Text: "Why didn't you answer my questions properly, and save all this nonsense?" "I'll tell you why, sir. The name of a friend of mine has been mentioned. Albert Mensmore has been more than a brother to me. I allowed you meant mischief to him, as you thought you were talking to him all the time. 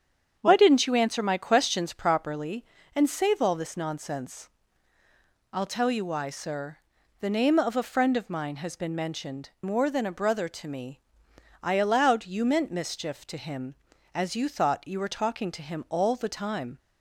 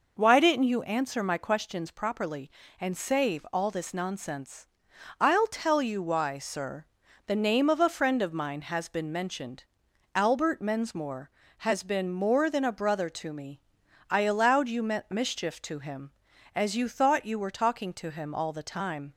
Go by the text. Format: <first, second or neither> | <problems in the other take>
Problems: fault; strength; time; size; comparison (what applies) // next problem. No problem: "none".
second | starts louder than the rest; strong; until 1.4 s; 8 dB // skips "Albert Mensmore has been"; at 9.5 s